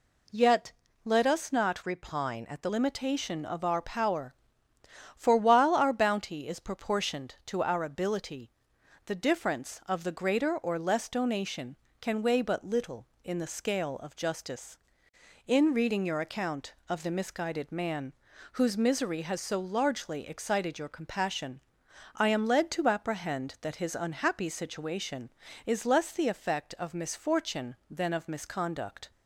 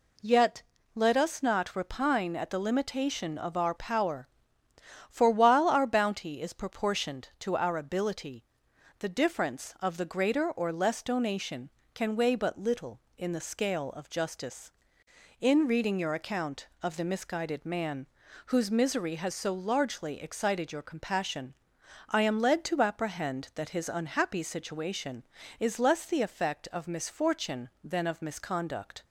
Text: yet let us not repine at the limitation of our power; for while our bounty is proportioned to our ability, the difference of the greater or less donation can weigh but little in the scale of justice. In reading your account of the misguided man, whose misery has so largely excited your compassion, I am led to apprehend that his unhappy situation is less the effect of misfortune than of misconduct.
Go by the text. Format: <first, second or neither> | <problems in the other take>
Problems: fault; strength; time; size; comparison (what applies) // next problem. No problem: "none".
second | pauses between "yet" and "let"; slight; at 0.7 s; 0.32 s long; slight in the second // changes voice from "repine" to "the"; from 1.8 to 2.6 s; 0.8 s long